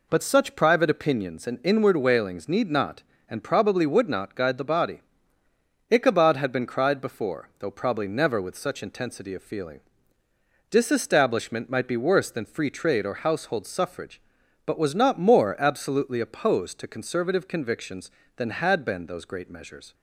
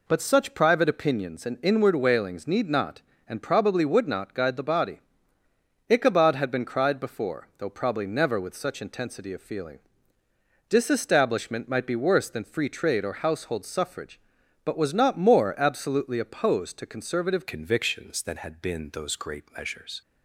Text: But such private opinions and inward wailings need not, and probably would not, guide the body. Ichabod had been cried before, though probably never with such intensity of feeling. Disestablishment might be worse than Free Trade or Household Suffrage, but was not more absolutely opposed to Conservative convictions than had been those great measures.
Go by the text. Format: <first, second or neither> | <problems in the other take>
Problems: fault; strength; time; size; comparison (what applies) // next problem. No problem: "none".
first | changes voice at "convictions"; from 17.4 s on; 2.6 s long